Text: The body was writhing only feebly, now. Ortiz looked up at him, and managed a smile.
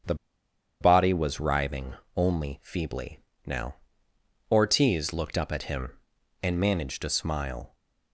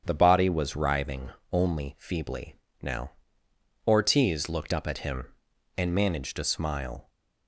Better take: second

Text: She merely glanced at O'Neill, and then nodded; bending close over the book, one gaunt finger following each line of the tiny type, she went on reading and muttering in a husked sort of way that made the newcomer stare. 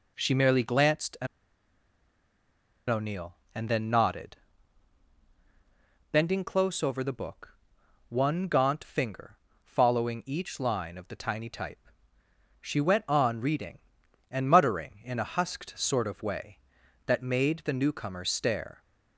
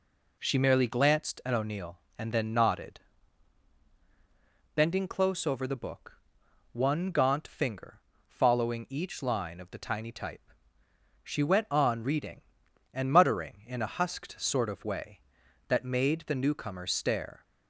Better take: second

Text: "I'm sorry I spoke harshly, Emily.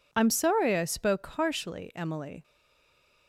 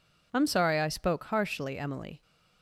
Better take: second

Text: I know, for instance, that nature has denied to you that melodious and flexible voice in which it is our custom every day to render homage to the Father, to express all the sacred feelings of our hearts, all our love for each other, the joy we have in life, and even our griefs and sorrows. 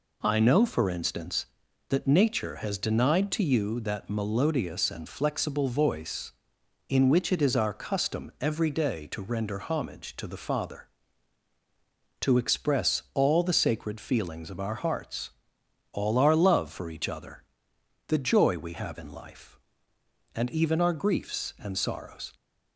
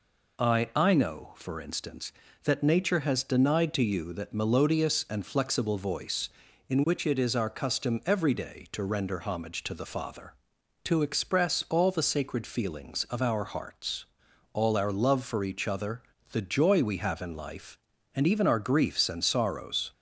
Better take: first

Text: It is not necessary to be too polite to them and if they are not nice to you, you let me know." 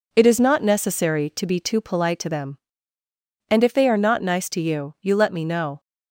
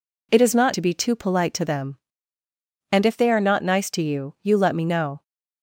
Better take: first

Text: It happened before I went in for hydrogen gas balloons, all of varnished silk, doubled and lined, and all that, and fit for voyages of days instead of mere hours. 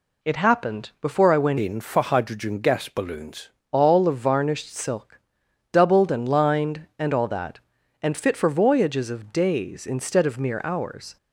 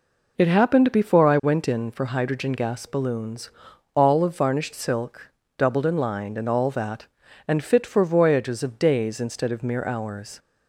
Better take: second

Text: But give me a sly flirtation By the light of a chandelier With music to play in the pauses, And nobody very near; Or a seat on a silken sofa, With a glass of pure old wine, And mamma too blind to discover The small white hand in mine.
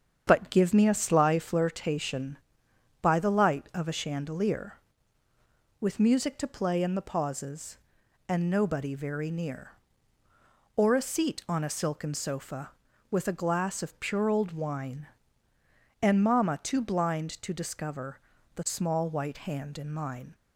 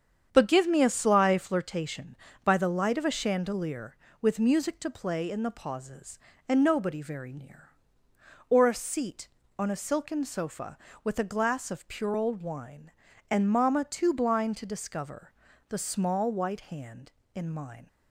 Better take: neither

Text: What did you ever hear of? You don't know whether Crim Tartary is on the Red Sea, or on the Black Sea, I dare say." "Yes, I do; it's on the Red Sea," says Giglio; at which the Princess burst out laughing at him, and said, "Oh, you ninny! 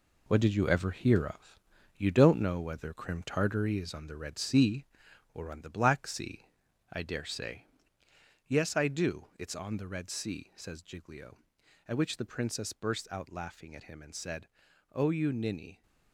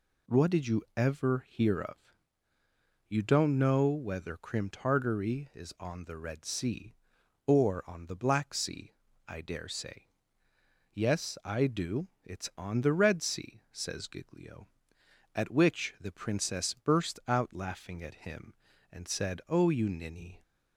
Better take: second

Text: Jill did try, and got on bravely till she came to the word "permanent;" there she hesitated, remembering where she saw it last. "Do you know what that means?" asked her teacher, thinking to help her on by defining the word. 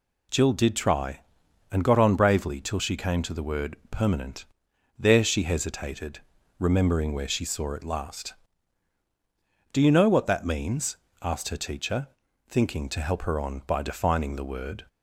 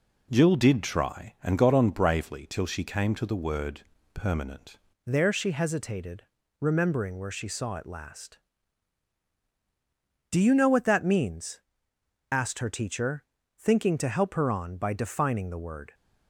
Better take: first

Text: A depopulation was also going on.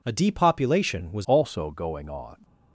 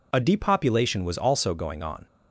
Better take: second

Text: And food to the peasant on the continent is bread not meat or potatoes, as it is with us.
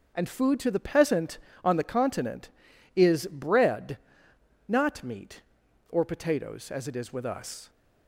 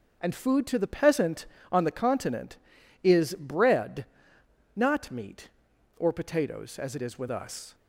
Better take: neither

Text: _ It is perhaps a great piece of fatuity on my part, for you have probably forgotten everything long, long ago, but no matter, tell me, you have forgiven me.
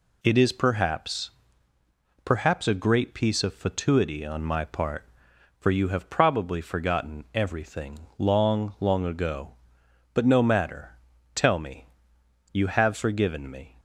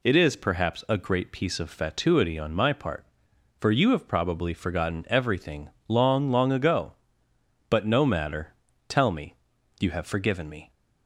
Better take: second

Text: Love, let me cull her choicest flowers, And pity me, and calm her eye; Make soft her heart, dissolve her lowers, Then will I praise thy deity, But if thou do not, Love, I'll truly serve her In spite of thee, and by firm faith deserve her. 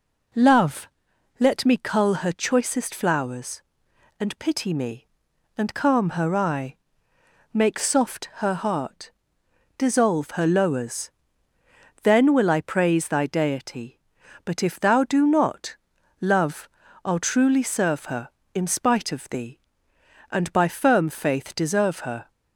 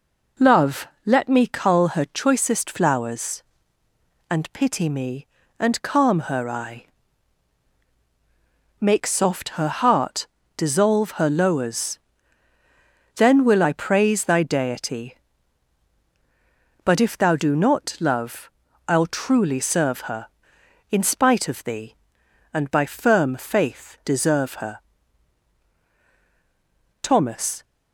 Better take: first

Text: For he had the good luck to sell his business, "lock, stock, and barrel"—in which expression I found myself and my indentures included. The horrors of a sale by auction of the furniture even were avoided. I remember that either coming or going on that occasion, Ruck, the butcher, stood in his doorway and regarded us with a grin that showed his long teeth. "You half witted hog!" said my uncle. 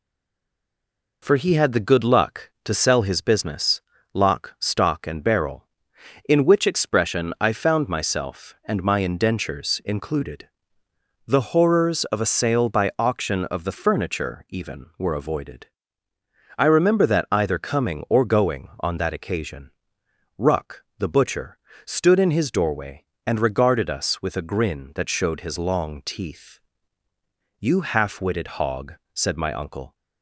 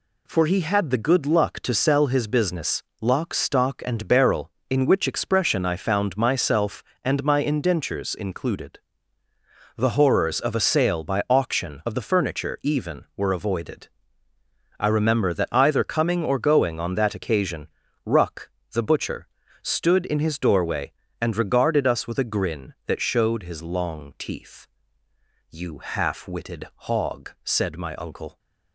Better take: second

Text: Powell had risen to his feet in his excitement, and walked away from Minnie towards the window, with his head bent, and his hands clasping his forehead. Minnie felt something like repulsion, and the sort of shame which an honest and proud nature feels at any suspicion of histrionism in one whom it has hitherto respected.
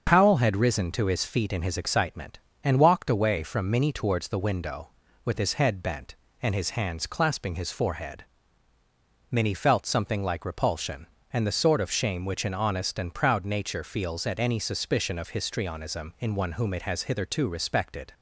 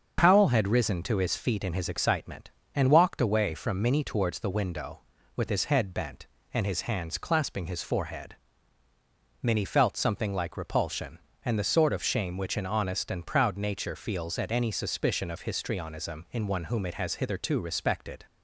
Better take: neither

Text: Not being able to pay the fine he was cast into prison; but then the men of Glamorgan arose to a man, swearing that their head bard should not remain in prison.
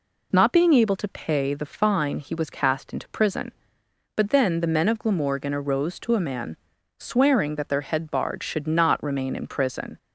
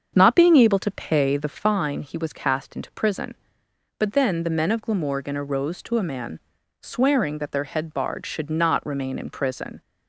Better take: first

